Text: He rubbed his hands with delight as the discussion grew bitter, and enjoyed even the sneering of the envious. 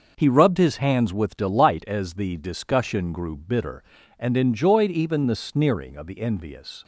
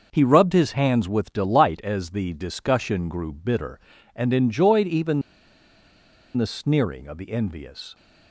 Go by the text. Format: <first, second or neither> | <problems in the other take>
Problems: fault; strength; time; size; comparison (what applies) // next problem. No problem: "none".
first | starts louder than the rest; noticeable; until 1.1 s; 6 dB; noticeable in the first // pauses between "even" and "the"; at 5.2 s; 1.1 s long